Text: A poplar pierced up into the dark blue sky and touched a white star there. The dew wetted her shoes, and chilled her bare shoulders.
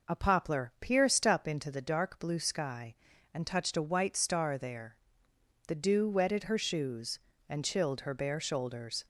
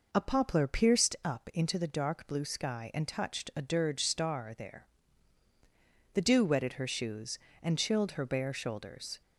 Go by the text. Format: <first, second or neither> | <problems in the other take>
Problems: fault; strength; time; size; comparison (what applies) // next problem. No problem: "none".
first | says "dirge" for "white"; at 3.6 s